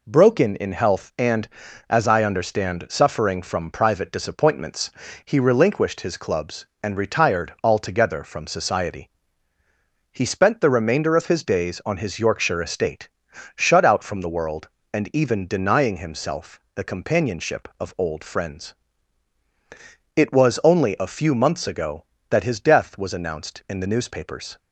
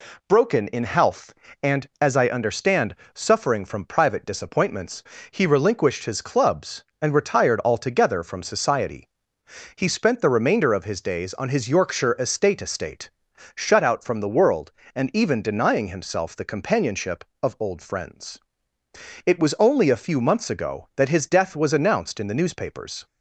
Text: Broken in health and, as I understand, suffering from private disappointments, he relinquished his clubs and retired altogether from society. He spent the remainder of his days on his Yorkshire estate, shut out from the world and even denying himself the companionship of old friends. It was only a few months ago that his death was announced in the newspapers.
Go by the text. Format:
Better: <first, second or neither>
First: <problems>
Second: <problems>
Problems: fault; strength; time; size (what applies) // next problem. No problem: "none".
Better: first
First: none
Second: says "estate" twice; at 12.6 s